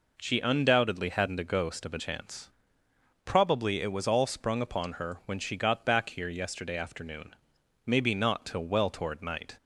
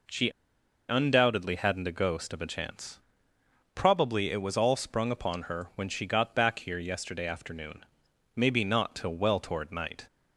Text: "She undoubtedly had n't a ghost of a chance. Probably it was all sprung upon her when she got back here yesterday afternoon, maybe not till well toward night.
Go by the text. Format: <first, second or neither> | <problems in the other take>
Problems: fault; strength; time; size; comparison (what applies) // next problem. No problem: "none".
first | pauses between "She" and "undoubtedly"; noticeable; at 0.2 s; 0.59 s long